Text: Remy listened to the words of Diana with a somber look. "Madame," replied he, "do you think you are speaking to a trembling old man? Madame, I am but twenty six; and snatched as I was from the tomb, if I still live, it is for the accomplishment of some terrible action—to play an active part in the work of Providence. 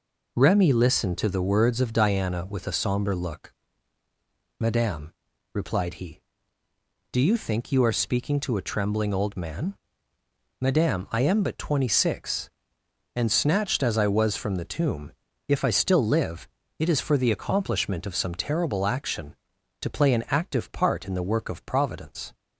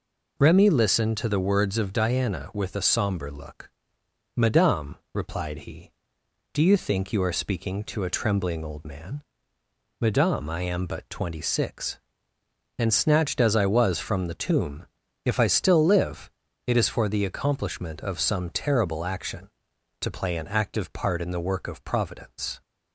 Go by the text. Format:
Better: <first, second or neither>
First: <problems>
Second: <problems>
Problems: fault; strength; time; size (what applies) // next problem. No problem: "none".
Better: neither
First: none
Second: none